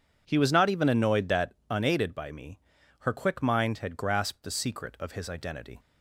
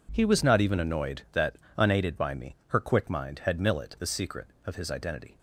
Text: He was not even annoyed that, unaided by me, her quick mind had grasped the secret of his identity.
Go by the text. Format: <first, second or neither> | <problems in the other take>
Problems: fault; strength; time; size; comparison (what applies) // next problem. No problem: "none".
first | says "millet" for "grasped"; at 3.5 s